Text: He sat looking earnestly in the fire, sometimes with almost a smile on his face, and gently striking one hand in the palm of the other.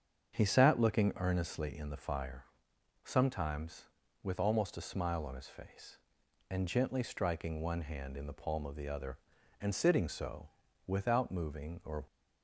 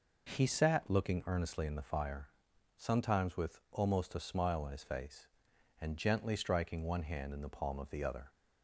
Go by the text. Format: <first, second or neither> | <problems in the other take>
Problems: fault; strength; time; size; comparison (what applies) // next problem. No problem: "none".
second | starts louder than the rest; strong; until 1.3 s; 7 dB // goes on to say "And sitting so without moving or"; strong; from 9.6 s on; 2.4 s long